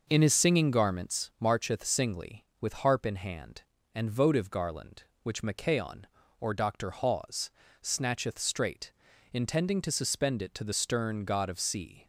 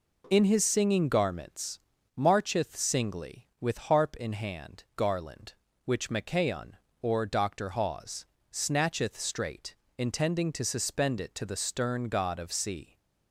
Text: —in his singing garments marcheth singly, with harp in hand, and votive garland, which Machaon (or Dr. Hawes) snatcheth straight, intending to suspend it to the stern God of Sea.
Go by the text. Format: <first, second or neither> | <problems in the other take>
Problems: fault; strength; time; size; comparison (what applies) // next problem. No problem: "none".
first | pauses between "garments" and "marcheth"; at 1.7 s; 0.38 s long // skips "and votive"; at 4.8 s